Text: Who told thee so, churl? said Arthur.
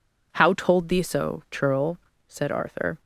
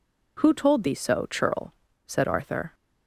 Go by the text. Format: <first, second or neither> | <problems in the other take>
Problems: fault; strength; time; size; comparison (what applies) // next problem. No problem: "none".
second | says "How" for "Who"; at 0.3 s